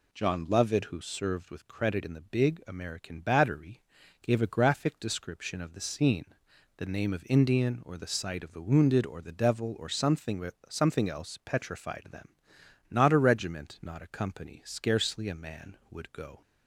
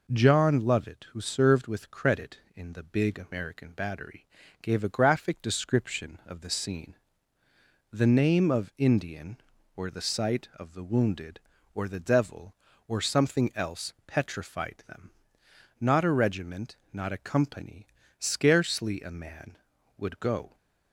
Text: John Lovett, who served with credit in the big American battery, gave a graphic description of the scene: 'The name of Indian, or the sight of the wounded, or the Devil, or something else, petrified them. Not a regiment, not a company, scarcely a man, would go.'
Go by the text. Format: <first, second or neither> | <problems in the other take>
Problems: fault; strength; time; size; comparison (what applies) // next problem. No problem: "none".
second | says "something" twice; at 10.6 s